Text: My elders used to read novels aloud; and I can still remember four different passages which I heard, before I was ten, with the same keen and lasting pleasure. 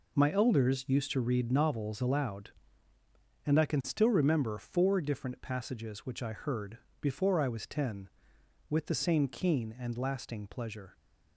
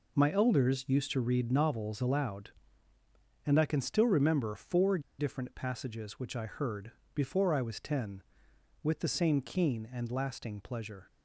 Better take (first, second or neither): first